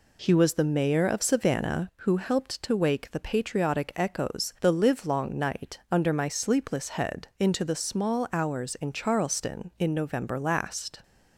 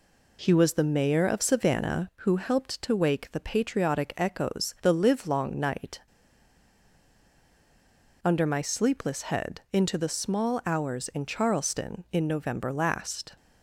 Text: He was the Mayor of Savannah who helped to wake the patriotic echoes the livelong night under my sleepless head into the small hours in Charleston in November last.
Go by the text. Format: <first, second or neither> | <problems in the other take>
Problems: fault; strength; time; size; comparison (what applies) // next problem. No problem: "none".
first | pauses between "night" and "under"; strong; at 5.9 s; 2.2 s long